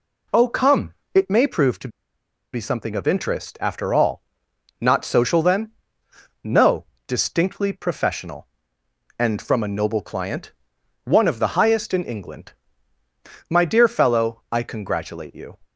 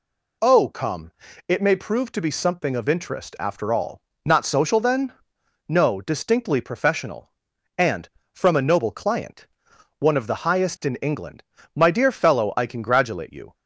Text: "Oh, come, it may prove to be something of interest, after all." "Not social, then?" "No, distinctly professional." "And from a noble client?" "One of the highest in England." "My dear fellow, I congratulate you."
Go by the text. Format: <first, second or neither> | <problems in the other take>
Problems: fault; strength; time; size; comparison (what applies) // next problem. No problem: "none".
second | pauses between "to" and "be"; noticeable; at 1.8 s; 0.65 s long